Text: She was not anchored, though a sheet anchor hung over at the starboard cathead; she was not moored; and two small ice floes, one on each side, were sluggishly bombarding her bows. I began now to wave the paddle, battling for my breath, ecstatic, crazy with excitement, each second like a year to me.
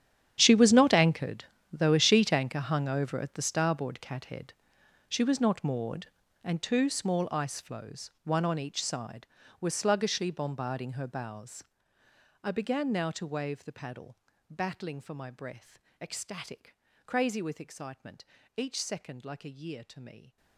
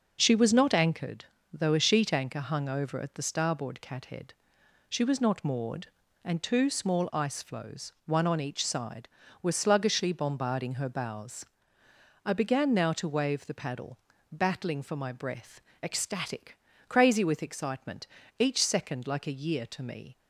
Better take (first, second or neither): second